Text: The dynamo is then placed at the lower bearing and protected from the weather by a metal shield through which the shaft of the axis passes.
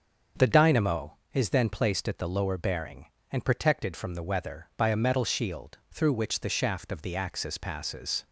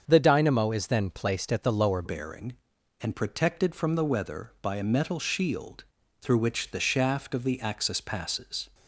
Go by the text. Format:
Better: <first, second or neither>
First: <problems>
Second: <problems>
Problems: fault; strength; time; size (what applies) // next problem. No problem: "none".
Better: first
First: starts louder than the rest; until 1.5 s; 6.5 dB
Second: starts louder than the rest; until 1.0 s; 7 dB // changes voice at "bearing"; from 2.0 s on; 6.6 s long // pauses between "shield" and "through"; slight; at 5.8 s; 0.36 s long